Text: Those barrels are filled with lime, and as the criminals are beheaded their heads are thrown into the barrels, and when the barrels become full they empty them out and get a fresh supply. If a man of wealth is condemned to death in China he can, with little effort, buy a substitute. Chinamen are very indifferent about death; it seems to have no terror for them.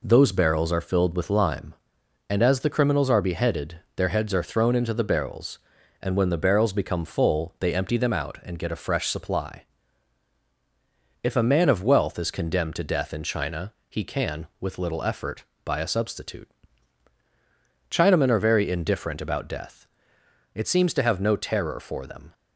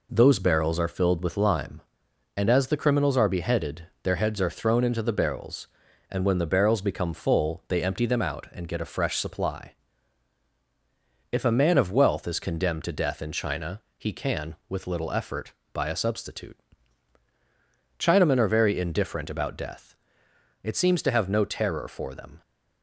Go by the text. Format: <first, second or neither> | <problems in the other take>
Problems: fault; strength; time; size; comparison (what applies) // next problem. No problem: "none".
neither | pauses between "beheaded" and "their"; slight; the same in both // pauses between "China" and "he"; slight; the same in both